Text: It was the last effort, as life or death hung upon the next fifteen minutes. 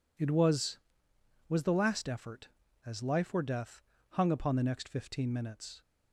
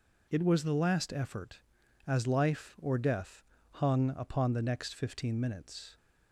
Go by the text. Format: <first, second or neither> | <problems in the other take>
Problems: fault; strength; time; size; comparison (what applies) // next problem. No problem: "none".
second | says "was" twice; at 1.4 s // pauses between "death" and "hung"; slight; at 3.8 s; 0.30 s long; slight in the second